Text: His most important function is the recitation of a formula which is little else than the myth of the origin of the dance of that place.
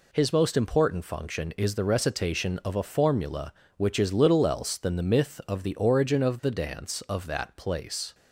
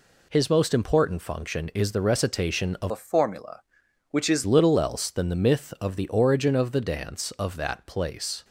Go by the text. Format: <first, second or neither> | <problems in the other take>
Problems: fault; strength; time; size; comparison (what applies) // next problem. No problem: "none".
first | changes voice from "a" to "is"; from 2.9 to 4.4 s; 1.5 s long